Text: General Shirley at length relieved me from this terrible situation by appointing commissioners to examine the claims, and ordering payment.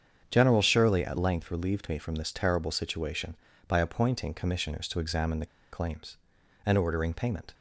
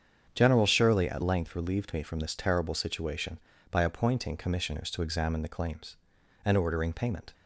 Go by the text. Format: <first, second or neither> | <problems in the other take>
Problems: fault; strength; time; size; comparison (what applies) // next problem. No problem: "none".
second | starts louder than the rest; strong; until 1.3 s; 7.5 dB; strong in the second // pauses between "the" and "claims"; slight; at 5.4 s; 0.25 s long